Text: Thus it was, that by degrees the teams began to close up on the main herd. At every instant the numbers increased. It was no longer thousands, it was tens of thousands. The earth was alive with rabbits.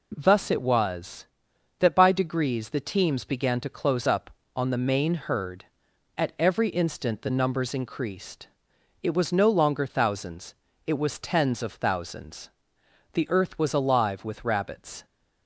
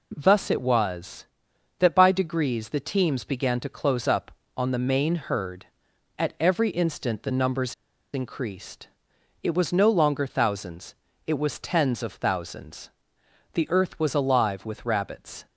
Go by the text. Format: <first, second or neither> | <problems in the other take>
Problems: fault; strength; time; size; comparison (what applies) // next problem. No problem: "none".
first | pauses between "numbers" and "increased"; at 7.7 s; 0.39 s long